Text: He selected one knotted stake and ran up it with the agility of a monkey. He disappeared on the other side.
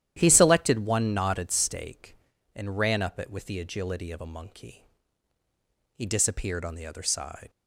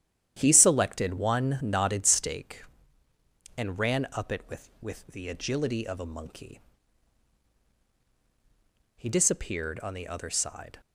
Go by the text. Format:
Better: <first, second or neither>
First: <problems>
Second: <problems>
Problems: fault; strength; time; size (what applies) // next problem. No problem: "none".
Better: first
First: starts louder than the rest; strong; until 1.1 s; 11.5 dB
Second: starts louder than the rest; strong; until 1.3 s; 10.5 dB // says "with" twice; at 4.8 s